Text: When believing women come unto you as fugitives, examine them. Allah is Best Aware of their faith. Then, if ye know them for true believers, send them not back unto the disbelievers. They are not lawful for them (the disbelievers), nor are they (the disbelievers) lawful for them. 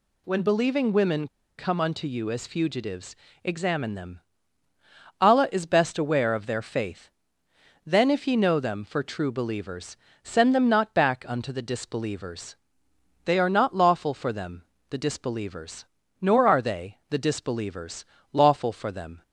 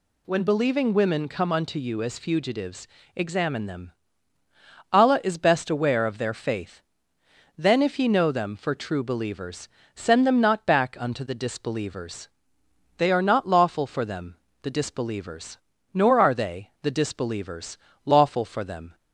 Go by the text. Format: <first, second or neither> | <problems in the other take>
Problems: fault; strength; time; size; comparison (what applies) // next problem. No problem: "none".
second | pauses between "women" and "come"; slight; at 1.2 s; 0.30 s long